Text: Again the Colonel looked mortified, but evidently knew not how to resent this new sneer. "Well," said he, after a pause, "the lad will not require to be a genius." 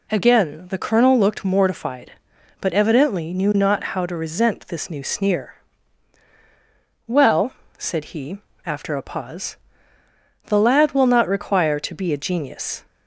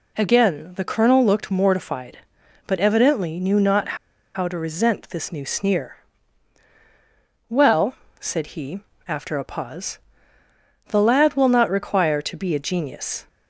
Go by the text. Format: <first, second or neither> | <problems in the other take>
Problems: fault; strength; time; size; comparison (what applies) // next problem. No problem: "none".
first | pauses between "not" and "how"; at 3.9 s; 0.38 s long